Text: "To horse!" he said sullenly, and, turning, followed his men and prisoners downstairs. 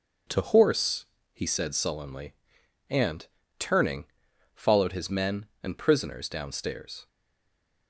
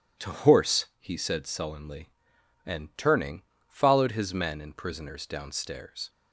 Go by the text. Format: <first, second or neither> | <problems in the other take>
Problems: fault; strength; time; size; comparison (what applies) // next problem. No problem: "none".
second | stays silent after the last word; slight; from 7.0 s on; 0.8 s long